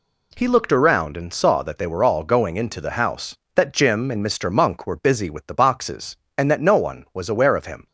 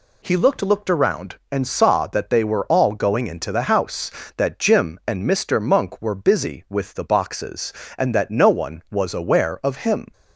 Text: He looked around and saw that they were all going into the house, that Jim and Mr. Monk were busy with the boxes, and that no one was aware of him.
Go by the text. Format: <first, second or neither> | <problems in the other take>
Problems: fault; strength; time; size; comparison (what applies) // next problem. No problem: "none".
first | says "looked" twice; at 0.6 s